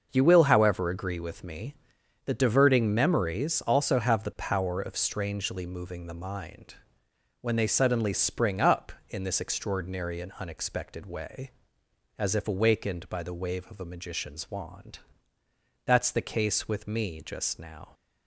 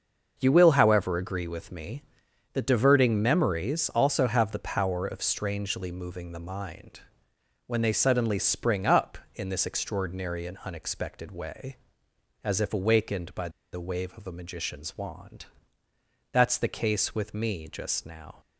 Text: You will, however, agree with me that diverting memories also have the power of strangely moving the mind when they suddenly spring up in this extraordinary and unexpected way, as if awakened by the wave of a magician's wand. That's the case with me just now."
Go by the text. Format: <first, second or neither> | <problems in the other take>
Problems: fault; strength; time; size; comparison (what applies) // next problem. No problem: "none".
first | starts louder than the rest; until 1.3 s; 6.5 dB; also in the first // pauses between "mind" and "when"; noticeable; at 7.0 s; 0.66 s long; noticeable in the first // pauses between "by" and "the"; slight; at 13.4 s; 0.23 s long